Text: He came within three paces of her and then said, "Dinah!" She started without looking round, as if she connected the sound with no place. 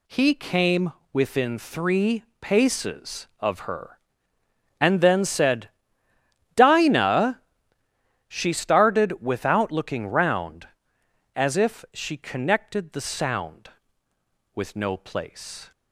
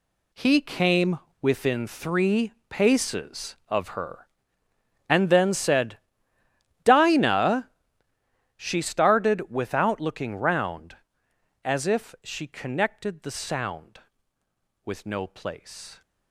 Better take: first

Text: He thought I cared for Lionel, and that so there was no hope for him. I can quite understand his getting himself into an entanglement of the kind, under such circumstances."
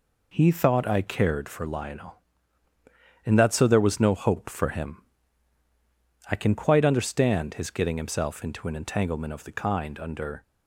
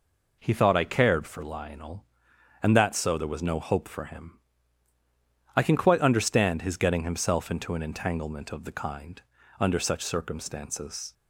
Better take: second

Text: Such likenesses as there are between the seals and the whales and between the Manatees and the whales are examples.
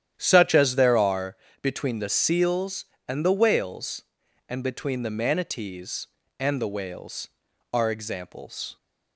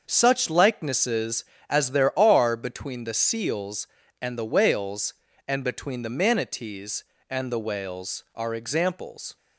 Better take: second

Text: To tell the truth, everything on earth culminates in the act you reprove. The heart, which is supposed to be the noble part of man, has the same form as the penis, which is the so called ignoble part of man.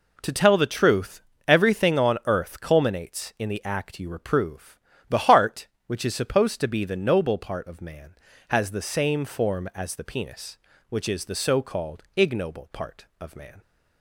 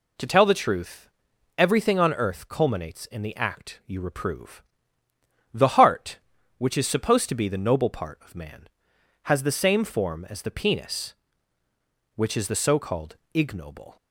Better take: first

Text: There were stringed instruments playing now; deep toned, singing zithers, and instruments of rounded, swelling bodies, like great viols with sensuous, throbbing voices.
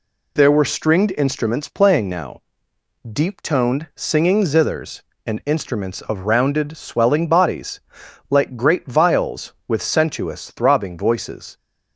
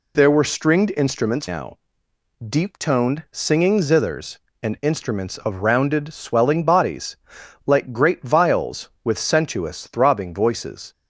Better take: first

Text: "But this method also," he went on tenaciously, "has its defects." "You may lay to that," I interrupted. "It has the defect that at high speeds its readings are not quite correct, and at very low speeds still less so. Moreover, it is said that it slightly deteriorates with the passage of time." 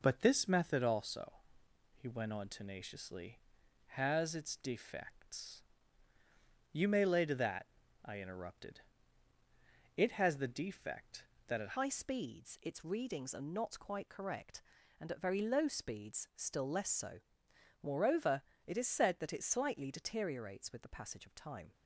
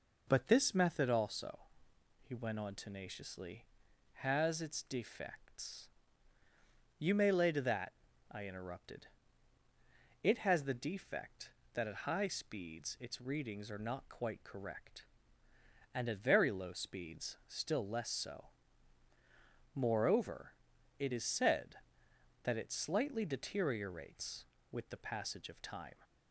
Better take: second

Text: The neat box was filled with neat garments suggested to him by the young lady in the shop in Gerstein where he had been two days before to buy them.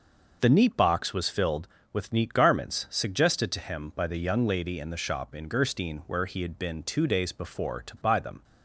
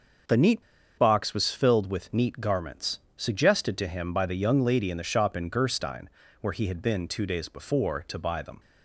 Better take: first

